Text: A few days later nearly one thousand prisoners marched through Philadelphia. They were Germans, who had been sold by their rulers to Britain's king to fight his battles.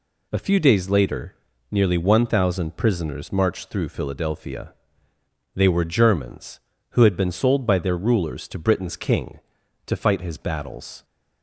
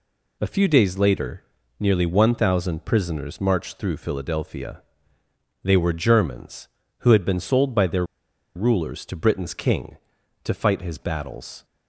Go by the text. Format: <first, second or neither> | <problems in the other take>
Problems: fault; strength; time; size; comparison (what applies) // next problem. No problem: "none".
first | pauses between "later" and "nearly"; at 1.4 s; 0.38 s long; also in the first // pauses between "their" and "rulers"; noticeable; at 8.0 s; 0.50 s long